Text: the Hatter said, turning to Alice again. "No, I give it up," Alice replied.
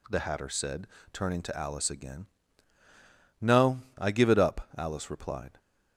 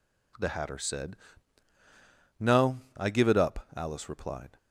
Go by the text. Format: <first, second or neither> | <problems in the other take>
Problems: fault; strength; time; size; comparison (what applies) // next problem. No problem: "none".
first | skips "turning to Alice again"; at 1.7 s